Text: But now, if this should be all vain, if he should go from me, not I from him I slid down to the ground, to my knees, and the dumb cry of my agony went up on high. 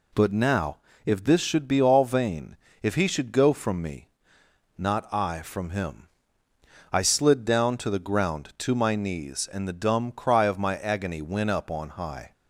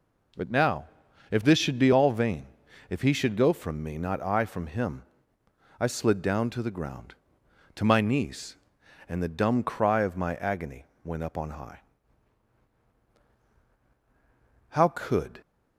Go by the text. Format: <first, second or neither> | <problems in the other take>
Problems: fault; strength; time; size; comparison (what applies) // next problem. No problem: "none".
first | pauses between "him" and "I"; noticeable; at 5.0 s; 0.76 s long; noticeable in the first // pauses between "agony" and "went"; slight; at 10.8 s; 0.18 s long // goes on to say "How could"; noticeable; from 14.7 s on; 0.70 s long